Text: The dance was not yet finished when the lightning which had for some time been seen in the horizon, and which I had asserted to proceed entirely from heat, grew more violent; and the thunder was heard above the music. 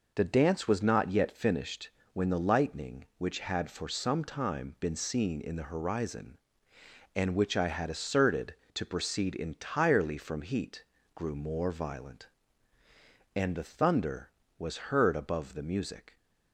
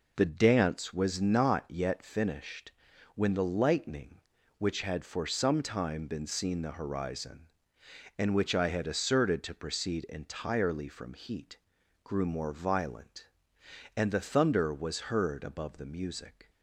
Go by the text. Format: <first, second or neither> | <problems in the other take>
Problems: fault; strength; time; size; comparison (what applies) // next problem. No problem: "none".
first | pauses between "finished" and "when"; at 2.7 s; 0.44 s long; slight in the first // skips "in"; at 6.6 s